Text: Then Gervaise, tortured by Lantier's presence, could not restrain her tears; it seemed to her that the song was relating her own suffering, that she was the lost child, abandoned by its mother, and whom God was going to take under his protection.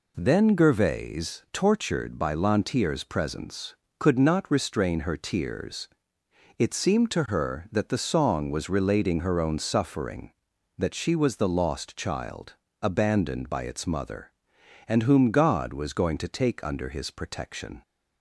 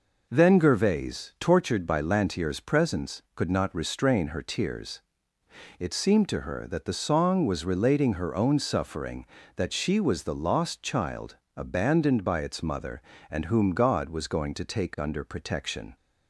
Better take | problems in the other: first | skips "his"; at 15.2 s

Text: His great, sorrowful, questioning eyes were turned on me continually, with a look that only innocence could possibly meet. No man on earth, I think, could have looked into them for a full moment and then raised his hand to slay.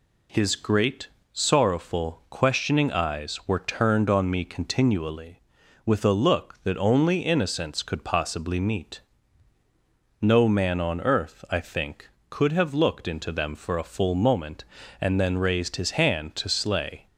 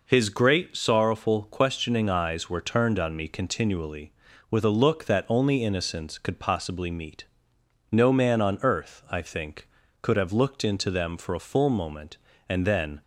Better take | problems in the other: first | stops before "raised his hand to slay"; at 13.0 s

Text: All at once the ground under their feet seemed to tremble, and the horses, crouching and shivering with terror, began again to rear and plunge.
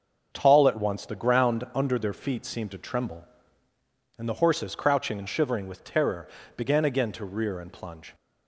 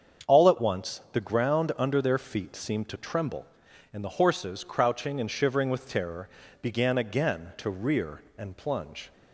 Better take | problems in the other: second | starts louder than the rest; until 1.3 s; 6.5 dB; strong in the second // says "Tall" for "All"; at 0.3 s

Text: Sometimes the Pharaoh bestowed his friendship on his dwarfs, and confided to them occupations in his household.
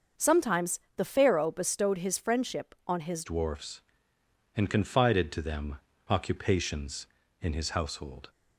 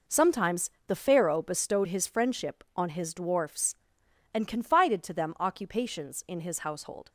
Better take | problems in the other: second | starts louder than the rest; until 1.3 s; 6 dB // pauses between "Sometimes" and "the"; slight; at 0.7 s; 0.18 s long; slight in the second // changes voice at "dwarfs"; from 3.2 s on; 5.0 s long // pauses between "them" and "occupations"; slight; at 5.8 s; 0.28 s long

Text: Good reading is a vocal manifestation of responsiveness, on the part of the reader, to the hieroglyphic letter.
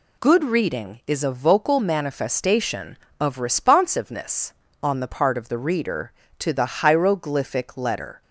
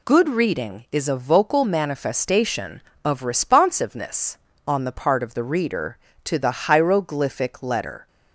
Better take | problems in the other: neither | none

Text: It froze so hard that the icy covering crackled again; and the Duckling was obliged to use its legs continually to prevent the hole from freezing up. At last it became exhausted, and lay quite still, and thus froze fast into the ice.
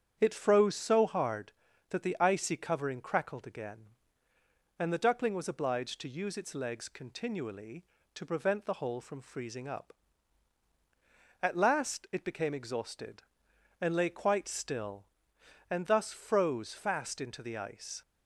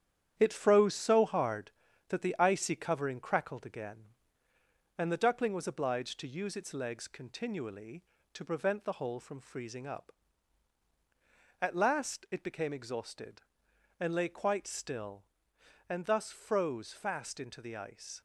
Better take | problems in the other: first | gets quieter; throughout; 6.5 dB // starts louder than the rest; strong; until 1.3 s; 9.5 dB; strong in the first

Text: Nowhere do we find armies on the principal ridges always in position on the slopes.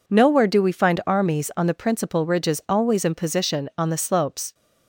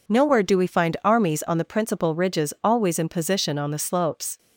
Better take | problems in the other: neither | none

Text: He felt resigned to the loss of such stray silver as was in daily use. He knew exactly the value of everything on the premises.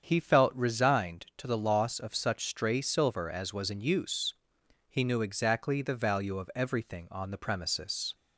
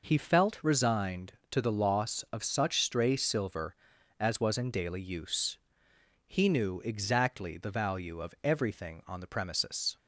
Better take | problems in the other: second | starts louder than the rest; strong; until 1.0 s; 7.5 dB // skips "daily"; at 3.8 s

